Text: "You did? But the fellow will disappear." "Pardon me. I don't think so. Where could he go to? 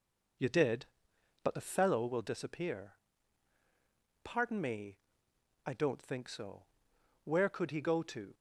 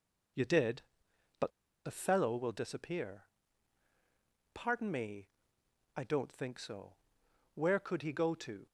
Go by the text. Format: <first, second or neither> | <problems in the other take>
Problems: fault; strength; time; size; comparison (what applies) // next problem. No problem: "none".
first | pauses between "But" and "the"; slight; at 1.4 s; 0.34 s long